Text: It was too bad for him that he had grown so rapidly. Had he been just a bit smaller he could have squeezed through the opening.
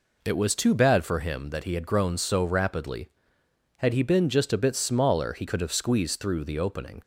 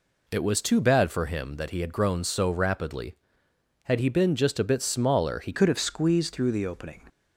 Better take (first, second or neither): first